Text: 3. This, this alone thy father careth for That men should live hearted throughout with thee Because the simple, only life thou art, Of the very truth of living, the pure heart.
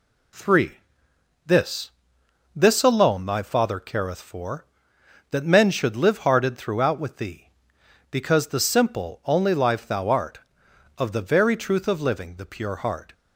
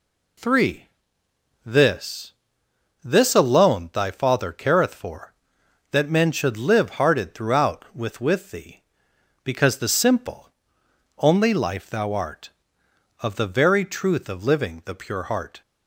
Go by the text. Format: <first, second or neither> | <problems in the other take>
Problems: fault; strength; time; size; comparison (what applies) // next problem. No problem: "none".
first | says "with" twice; at 8.2 s